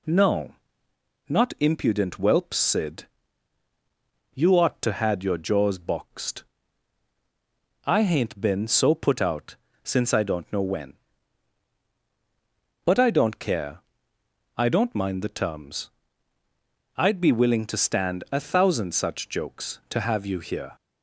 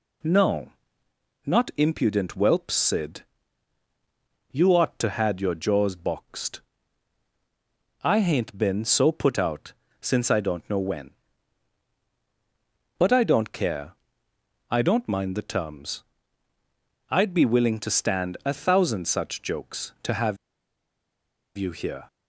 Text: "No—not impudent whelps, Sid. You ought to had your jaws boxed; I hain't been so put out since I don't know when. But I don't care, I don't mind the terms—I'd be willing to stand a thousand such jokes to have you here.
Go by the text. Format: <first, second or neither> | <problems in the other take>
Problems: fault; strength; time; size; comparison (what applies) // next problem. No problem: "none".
first | pauses between "out" and "since"; slight; at 9.7 s; 0.26 s long; slight in the first // pauses between "have" and "you"; at 20.3 s; 1.1 s long